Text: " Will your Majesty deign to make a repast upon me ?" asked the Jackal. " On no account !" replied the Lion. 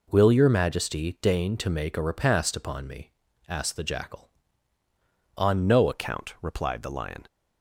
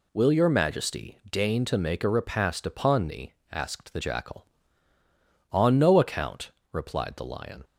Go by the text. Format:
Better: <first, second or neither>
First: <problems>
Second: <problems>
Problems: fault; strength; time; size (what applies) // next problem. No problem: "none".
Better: second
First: changes voice at "account"; from 5.9 s on; 1.3 s long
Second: none